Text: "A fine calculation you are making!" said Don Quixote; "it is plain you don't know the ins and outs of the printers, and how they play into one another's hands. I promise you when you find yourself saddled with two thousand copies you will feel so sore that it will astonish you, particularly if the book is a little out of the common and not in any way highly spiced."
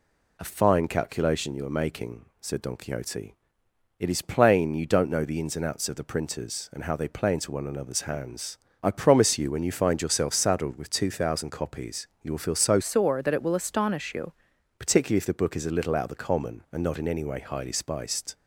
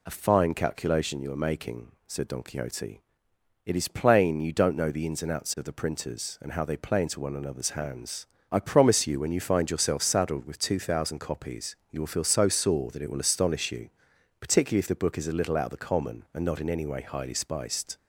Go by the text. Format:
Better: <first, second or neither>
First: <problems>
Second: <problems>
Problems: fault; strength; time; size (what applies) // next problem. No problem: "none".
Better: second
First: changes voice from "sore" to "you"; from 12.8 to 14.3 s; 1.5 s long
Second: none